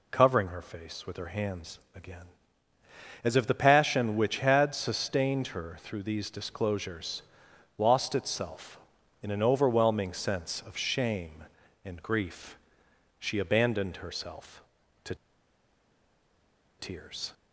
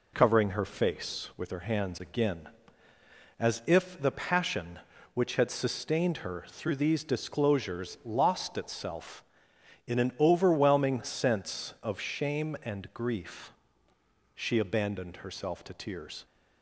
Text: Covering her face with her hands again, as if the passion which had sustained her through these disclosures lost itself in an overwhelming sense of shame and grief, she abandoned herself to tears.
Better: second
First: pauses between "hands" and "again"; slight; at 1.7 s; 0.16 s long // pauses between "disclosures" and "lost"; noticeable; at 7.2 s; 0.56 s long // pauses between "to" and "tears"; strong; at 15.1 s; 1.6 s long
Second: none

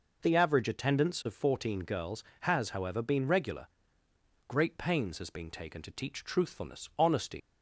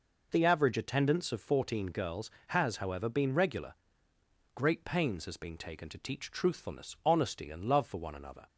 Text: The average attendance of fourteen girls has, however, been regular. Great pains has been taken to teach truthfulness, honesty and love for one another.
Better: second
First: stops before "and love for one another"; at 7.4 s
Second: none

